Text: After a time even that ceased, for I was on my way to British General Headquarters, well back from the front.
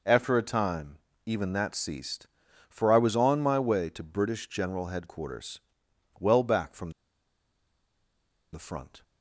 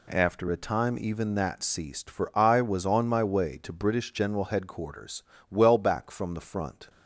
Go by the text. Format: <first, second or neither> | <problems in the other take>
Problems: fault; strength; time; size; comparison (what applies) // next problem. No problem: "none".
second | pauses between "time" and "even"; slight; at 0.9 s; 0.30 s long // pauses between "from" and "the"; strong; at 6.9 s; 1.6 s long